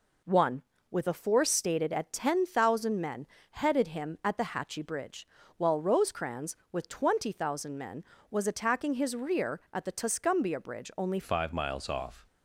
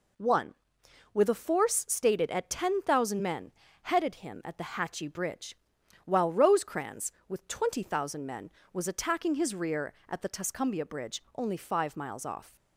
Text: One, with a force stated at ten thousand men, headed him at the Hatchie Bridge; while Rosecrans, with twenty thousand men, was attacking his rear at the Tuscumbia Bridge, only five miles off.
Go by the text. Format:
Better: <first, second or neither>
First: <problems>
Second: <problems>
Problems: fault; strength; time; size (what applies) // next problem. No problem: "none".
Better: second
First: changes voice at "five"; from 11.2 s on; 1.0 s long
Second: none